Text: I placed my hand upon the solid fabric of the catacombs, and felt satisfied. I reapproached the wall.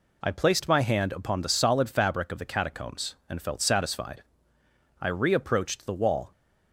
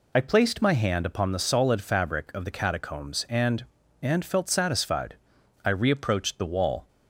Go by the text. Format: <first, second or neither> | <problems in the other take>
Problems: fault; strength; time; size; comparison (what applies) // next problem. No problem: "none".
first | says "and" twice; at 4.0 s